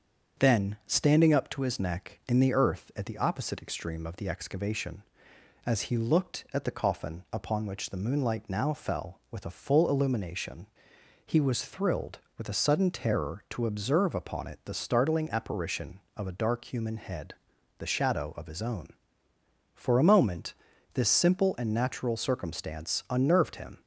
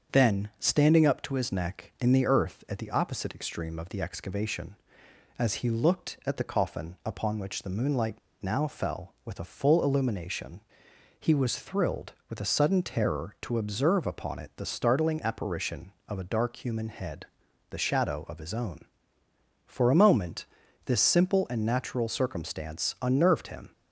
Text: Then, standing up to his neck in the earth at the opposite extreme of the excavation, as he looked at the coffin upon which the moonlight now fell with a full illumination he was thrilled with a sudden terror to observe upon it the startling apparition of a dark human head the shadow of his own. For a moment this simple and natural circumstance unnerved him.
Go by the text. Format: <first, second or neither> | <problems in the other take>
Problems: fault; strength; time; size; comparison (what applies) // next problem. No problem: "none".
first | starts louder than the rest; strong; until 1.2 s; 7 dB; strong in the first // pauses between "moonlight" and "now"; slight; at 8.1 s; 0.22 s long // pauses between "illumination" and "he"; noticeable; at 10.5 s; 0.60 s long; noticeable in the first // pauses between "head" and "the"; at 17.2 s; 0.44 s long; also in the first // pauses between "moment" and "this"; at 20.4 s; 0.40 s long; also in the first